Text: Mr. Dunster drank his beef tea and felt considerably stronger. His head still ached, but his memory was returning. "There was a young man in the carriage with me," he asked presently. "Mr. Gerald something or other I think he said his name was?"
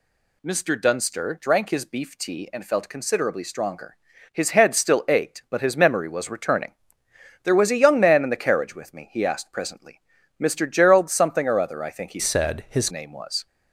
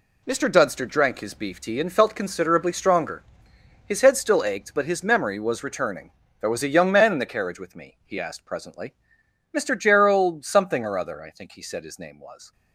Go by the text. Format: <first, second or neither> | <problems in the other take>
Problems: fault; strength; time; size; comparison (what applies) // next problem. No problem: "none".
second | changes voice from "said" to "his"; from 12.1 to 12.9 s; 0.8 s long